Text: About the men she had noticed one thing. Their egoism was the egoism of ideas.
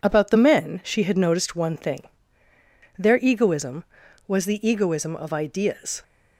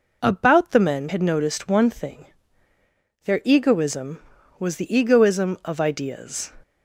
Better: first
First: none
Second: skips "she"; at 1.0 s

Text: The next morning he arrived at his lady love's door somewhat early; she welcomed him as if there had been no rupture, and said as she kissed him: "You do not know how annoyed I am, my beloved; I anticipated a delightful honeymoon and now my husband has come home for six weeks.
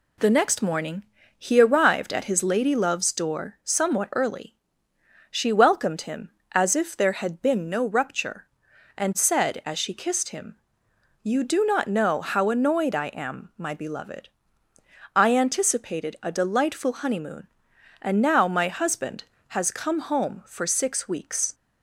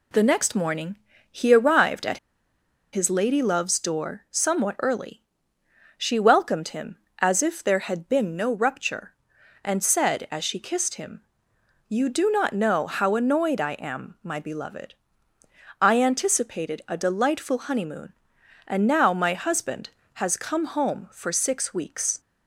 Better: first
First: pauses between "morning" and "he"; slight; at 1.0 s; 0.32 s long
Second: pauses between "morning" and "he"; slight; at 0.9 s; 0.32 s long // pauses between "at" and "his"; noticeable; at 2.1 s; 0.74 s long

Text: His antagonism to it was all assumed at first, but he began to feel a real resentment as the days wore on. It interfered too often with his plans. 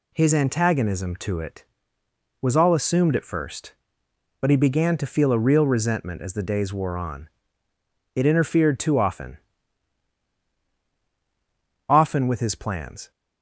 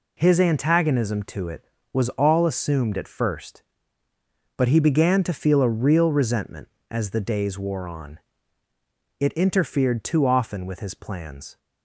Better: second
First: says "often" twice; at 11.8 s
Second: none

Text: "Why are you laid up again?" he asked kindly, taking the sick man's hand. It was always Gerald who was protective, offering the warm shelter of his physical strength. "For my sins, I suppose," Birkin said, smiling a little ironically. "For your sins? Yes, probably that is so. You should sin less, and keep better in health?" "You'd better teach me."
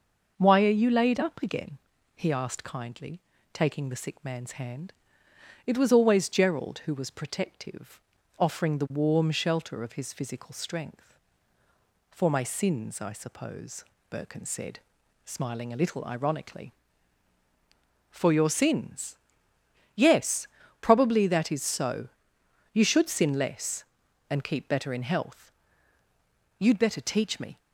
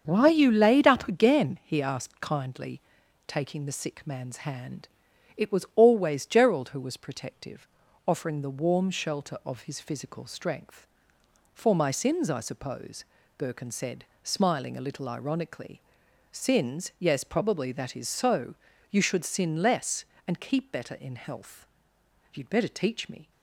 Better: first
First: none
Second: starts louder than the rest; until 1.0 s; 7 dB // skips "For your"; at 16.0 s

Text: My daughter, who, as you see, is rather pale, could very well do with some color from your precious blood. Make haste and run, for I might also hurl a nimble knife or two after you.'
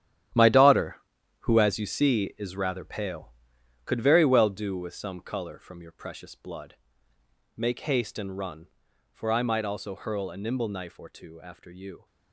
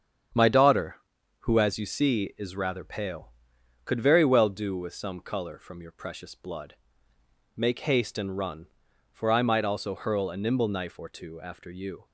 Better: second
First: gets quieter; strong; throughout; 12.5 dB // starts louder than the rest; strong; until 1.8 s; 11.5 dB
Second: starts louder than the rest; strong; until 1.8 s; 8 dB

